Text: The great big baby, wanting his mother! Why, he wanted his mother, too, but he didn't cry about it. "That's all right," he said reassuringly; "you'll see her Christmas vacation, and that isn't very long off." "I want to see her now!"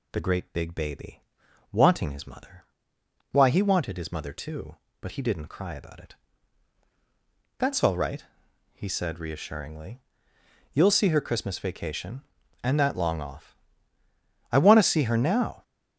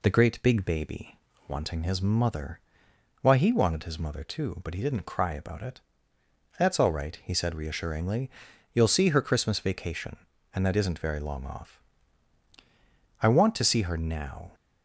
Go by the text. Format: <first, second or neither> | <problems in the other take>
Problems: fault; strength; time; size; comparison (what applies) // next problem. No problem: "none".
second | skips "isn't very"; at 12.9 s